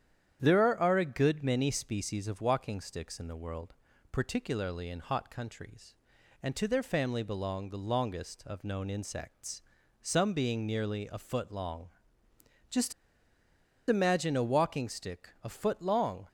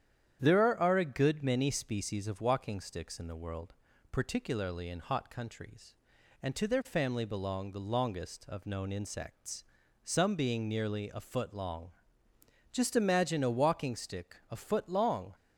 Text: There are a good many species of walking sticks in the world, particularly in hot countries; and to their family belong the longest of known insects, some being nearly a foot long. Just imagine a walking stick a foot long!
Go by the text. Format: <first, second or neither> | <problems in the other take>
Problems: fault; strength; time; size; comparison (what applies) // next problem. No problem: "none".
second | starts louder than the rest; strong; until 1.4 s; 9.5 dB; strong in the second // pauses between "Just" and "imagine"; noticeable; at 12.9 s; 0.96 s long // pauses between "stick" and "a"; slight; at 15.2 s; 0.16 s long; slight in the second